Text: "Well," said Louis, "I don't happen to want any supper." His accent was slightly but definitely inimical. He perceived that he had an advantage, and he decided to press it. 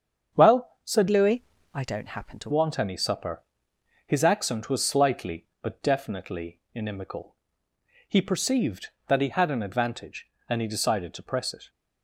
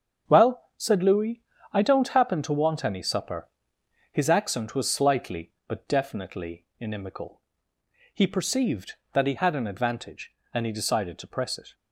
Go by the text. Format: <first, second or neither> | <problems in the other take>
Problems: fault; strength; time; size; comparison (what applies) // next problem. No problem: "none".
second | starts louder than the rest; strong; until 1.4 s; 7.5 dB; also in the second // changes voice from "Louis" to "to"; from 1.0 to 2.5 s; 1.5 s long